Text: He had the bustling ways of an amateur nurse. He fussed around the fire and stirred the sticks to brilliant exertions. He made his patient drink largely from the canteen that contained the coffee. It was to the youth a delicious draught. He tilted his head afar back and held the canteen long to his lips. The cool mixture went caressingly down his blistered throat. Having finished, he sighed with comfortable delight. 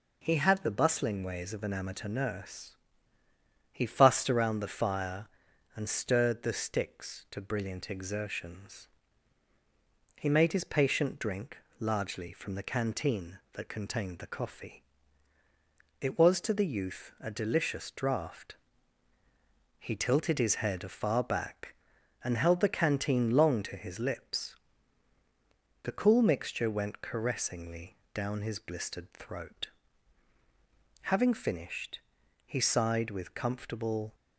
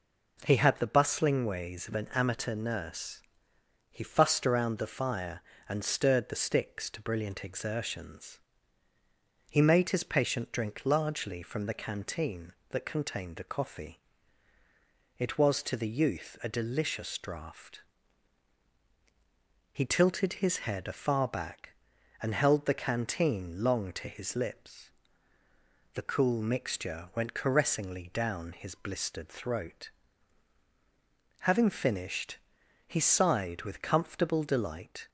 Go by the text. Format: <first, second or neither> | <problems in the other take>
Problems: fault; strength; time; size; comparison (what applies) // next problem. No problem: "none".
second | pauses between "drink" and "largely"; slight; at 11.5 s; 0.22 s long // pauses between "caressingly" and "down"; slight; at 27.9 s; 0.18 s long // stops before "delight"; at 34.1 s